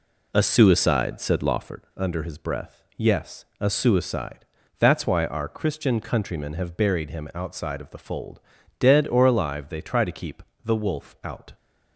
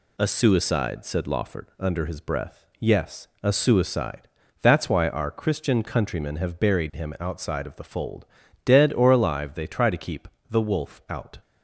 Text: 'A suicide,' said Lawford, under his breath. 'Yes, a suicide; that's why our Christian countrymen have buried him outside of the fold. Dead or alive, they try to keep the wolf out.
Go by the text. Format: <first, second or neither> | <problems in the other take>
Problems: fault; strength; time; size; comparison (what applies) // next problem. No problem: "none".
second | starts louder than the rest; slight; until 1.8 s; 3 dB // pauses between "keep" and "the"; slight; at 10.4 s; 0.22 s long; slight in the second